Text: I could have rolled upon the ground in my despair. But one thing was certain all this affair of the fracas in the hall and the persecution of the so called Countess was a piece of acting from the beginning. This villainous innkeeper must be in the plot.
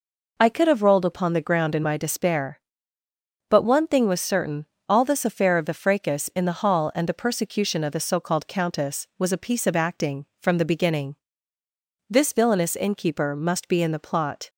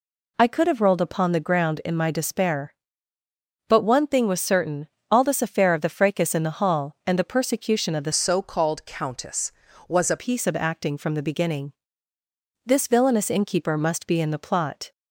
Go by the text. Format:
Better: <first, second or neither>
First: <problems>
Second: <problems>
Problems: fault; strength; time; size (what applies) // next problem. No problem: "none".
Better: first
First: pauses between "certain" and "all"; slight; at 4.6 s; 0.24 s long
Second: pauses between "certain" and "all"; slight; at 4.8 s; 0.22 s long // changes voice from "so" to "a"; from 8.1 to 10.1 s; 2.0 s long